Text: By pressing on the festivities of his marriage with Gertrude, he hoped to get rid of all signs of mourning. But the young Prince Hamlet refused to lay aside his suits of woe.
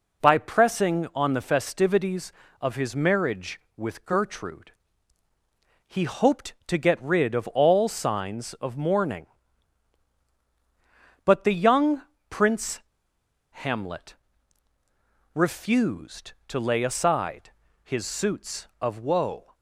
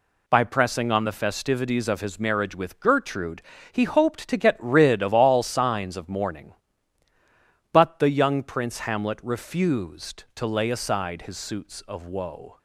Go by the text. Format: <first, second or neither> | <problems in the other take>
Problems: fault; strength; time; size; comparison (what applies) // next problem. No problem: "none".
second | pauses between "young" and "Prince"; slight; at 12.0 s; 0.26 s long // pauses between "Prince" and "Hamlet"; noticeable; at 12.7 s; 0.72 s long // pauses between "Hamlet" and "refused"; at 14.1 s; 1.2 s long // pauses between "aside" and "his"; slight; at 17.4 s; 0.32 s long